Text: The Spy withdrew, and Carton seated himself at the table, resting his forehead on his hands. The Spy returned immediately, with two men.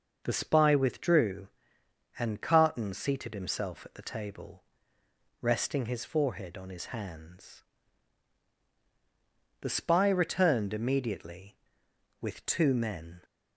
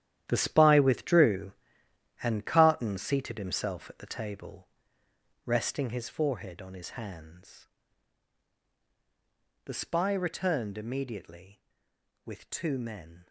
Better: first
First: none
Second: gets quieter; strong; throughout; 12.5 dB

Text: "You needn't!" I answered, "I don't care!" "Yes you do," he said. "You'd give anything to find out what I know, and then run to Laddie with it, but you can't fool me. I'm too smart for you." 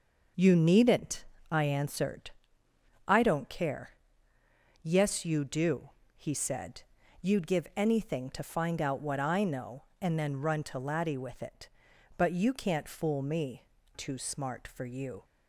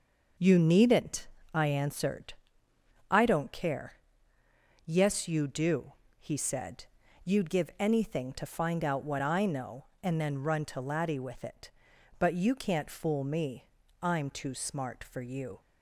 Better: second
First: skips "I'm"; at 13.7 s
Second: none

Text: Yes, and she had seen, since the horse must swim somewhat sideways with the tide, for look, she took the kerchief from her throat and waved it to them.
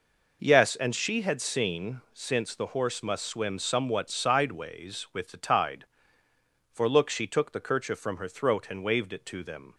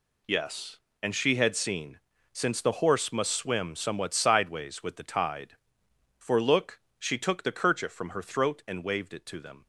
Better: neither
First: none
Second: none

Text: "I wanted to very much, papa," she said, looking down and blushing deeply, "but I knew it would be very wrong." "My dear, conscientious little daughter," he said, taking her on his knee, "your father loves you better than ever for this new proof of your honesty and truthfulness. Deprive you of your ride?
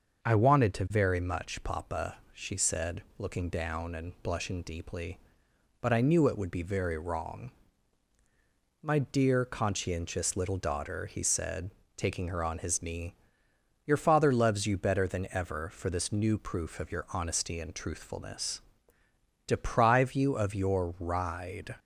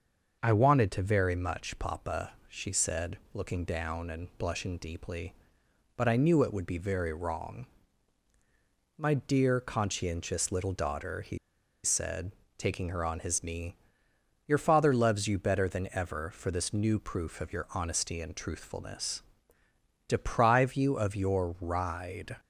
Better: first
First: starts louder than the rest; until 1.2 s; 6.5 dB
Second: starts louder than the rest; until 1.4 s; 6.5 dB // pauses between "he" and "said"; noticeable; at 11.3 s; 0.46 s long

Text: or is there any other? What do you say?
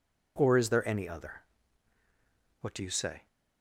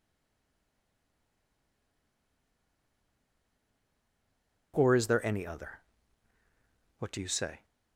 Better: first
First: none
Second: stays silent before the first word; strong; until 4.7 s; 4.7 s long

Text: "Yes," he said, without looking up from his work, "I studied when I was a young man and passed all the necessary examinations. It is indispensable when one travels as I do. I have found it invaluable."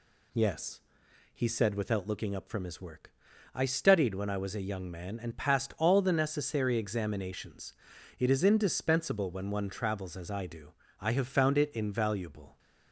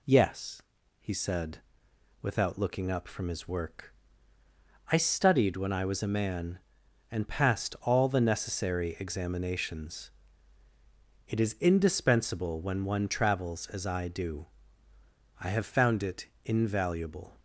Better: first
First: none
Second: skips "young"; at 6.1 s // pauses between "it" and "invaluable"; slight; at 16.2 s; 0.16 s long

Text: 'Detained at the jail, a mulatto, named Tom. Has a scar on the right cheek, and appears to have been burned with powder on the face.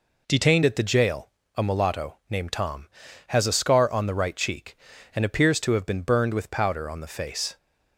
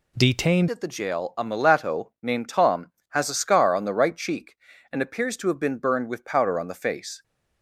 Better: first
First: none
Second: changes voice at "at"; from 0.6 s on; 6.6 s long

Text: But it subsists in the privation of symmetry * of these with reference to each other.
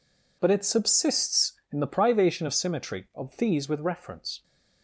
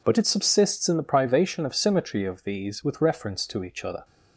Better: second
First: stops before "to each other"; at 4.4 s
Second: none

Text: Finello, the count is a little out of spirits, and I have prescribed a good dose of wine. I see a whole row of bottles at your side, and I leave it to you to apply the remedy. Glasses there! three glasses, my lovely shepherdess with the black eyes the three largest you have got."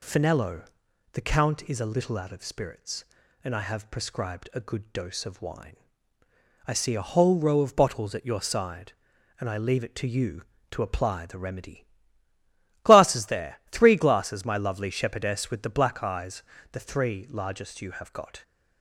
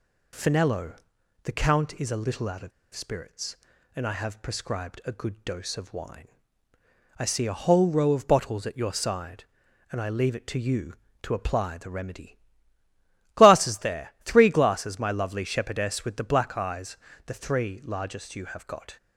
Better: first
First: pauses between "eyes" and "the"; slight; at 16.4 s; 0.30 s long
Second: pauses between "of" and "spirits"; slight; at 2.7 s; 0.23 s long // pauses between "eyes" and "the"; slight; at 16.9 s; 0.30 s long

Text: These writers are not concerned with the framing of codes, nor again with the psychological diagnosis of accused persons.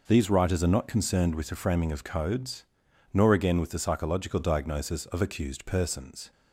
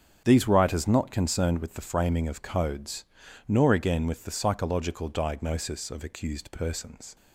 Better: first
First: none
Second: starts louder than the rest; strong; until 1.2 s; 7.5 dB // skips "are"; at 0.8 s

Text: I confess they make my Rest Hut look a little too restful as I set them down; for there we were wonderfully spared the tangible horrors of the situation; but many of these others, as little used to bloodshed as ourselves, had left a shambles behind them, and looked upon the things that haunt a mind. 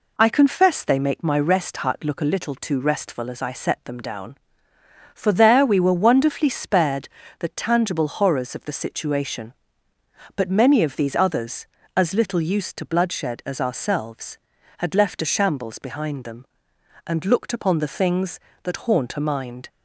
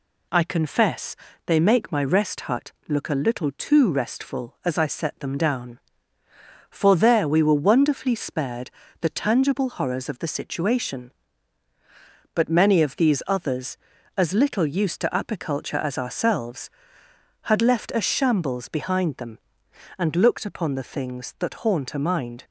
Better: first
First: pauses between "spared" and "the"; slight; at 7.0 s; 0.34 s long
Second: pauses between "confess" and "they"; slight; at 1.1 s; 0.30 s long // pauses between "spared" and "the"; slight; at 8.7 s; 0.30 s long // says "apiculture" for "bloodshed"; at 15.1 s

